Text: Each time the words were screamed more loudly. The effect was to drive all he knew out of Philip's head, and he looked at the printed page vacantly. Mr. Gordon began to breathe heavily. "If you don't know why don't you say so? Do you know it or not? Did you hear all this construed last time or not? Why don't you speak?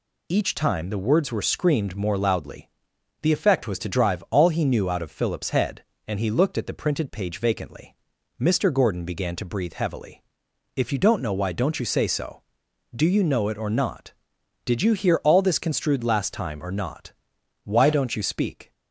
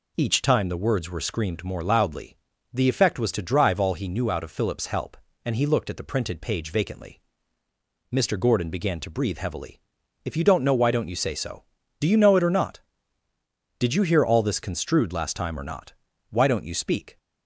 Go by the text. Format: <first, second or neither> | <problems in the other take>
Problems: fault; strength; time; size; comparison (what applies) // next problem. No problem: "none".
first | says "help" for "head"; at 4.8 s